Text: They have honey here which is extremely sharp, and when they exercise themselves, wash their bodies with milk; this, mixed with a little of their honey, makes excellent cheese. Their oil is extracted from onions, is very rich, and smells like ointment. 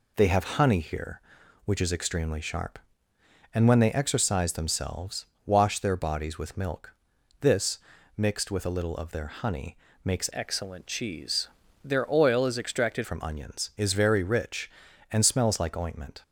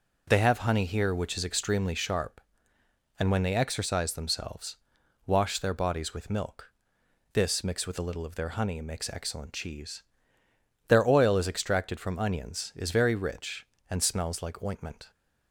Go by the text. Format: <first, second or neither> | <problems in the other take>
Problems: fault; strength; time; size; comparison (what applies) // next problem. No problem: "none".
second | changes voice from "excellent" to "extracted"; from 10.3 to 13.0 s; 2.7 s long